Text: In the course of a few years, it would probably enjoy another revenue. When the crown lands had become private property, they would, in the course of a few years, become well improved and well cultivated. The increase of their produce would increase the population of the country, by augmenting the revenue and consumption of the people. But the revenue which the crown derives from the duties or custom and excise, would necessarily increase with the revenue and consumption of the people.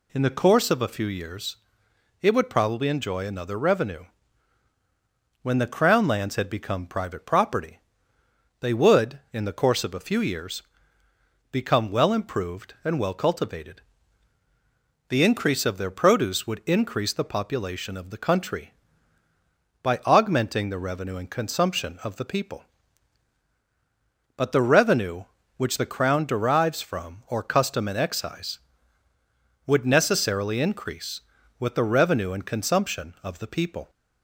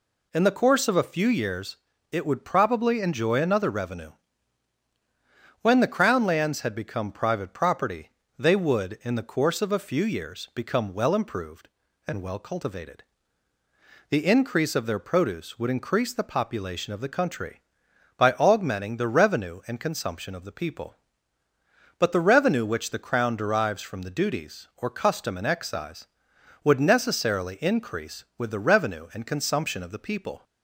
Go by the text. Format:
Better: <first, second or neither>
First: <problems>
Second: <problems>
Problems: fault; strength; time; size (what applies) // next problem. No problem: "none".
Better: second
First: skips "the duties"; at 27.2 s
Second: none